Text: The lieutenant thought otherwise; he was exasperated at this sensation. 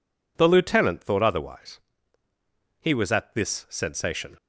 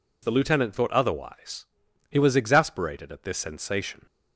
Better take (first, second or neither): second